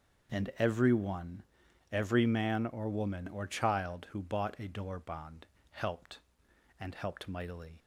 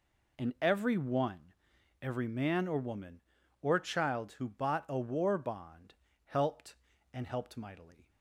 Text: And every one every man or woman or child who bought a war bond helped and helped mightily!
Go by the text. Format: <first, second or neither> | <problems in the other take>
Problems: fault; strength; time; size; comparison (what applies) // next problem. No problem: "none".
second | starts louder than the rest; until 1.4 s; 6.5 dB // pauses between "one" and "every"; noticeable; at 1.4 s; 0.50 s long; noticeable in the second // says "door" for "war"; at 4.6 s // pauses between "bond" and "helped"; slight; at 5.4 s; 0.28 s long; slight in the second